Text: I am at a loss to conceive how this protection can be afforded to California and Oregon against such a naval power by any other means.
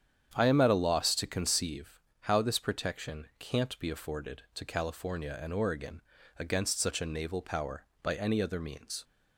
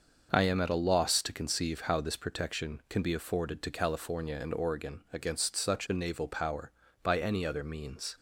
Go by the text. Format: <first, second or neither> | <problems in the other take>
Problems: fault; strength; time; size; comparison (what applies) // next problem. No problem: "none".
second | starts louder than the rest; strong; until 1.3 s; 8.5 dB; also in the second // pauses between "conceive" and "how"; slight; at 2.0 s; 0.20 s long // says "can't" for "can"; at 3.3 s // pauses between "Oregon" and "against"; at 6.0 s; 0.38 s long